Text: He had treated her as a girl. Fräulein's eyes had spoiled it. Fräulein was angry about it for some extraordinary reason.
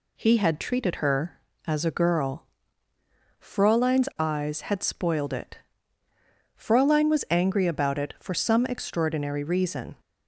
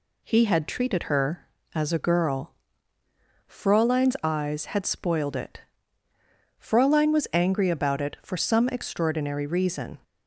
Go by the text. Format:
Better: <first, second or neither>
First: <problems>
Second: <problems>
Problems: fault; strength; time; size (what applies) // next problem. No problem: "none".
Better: neither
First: none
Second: none